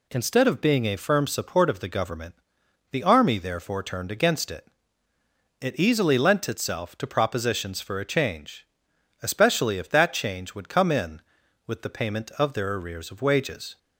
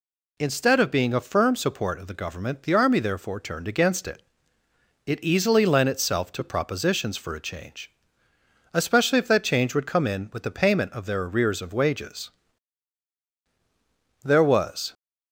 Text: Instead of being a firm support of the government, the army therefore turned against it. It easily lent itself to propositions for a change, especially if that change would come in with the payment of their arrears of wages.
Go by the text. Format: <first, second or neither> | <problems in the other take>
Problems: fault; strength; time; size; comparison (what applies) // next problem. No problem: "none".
first | goes on to say "There was"; noticeable; from 14.2 s on; 0.70 s long